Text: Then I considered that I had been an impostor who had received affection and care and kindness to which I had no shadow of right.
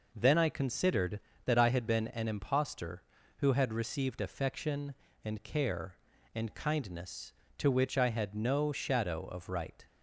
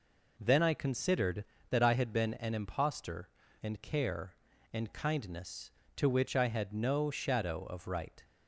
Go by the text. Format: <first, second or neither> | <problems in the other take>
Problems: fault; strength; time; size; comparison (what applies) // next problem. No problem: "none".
first | skips "who had received affection"; at 3.4 s